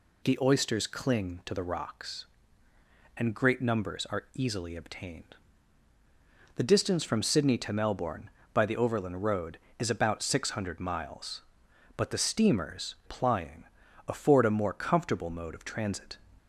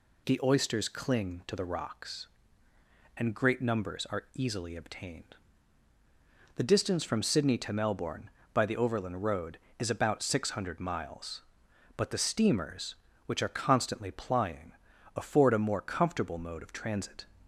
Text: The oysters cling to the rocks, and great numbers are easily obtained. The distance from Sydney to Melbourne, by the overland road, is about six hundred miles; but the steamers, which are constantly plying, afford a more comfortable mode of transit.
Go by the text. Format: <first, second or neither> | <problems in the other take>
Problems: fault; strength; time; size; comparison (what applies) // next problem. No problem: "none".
second | skips "which are constantly"; at 13.0 s